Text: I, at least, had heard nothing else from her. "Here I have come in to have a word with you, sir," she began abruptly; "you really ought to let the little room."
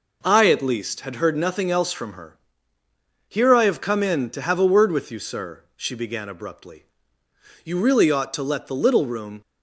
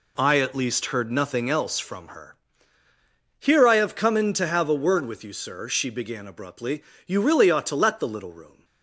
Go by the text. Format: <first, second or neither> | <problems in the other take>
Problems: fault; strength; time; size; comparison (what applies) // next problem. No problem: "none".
first | skips "had"; at 0.8 s